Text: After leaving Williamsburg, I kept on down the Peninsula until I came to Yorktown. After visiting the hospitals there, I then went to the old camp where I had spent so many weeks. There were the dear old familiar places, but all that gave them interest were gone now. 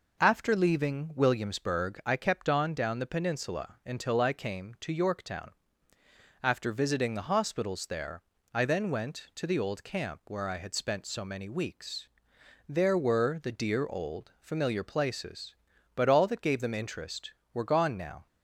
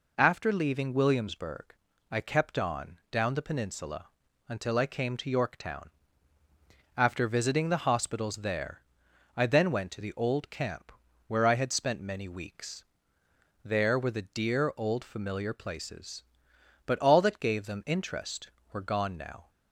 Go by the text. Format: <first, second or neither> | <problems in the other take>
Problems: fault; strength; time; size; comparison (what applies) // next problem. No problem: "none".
first | pauses between "Peninsula" and "until"; at 4.0 s; 0.38 s long // pauses between "camp" and "where"; slight; at 10.9 s; 0.34 s long // skips "so"; at 11.9 s